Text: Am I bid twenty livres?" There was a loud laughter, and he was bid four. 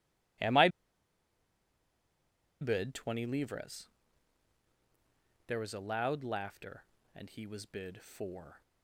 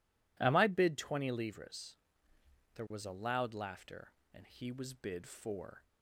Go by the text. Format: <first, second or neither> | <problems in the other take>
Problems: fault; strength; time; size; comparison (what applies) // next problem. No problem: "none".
second | pauses between "I" and "bid"; strong; at 0.6 s; 1.9 s long